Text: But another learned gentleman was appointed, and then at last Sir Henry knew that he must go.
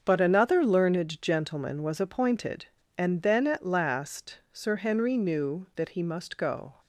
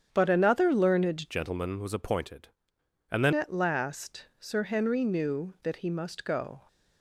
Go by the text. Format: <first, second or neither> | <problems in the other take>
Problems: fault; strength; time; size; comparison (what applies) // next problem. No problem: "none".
first | starts louder than the rest; strong; until 1.1 s; 8 dB; also in the first // changes voice from "gentleman" to "then"; from 1.3 to 3.3 s; 2.0 s long